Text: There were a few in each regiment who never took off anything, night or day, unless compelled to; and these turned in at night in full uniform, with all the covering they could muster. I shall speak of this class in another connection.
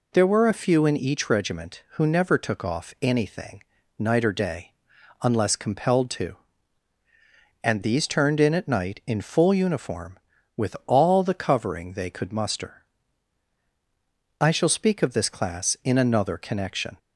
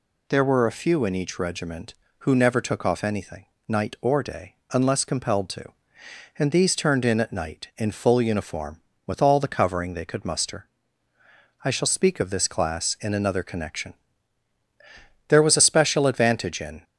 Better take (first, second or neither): first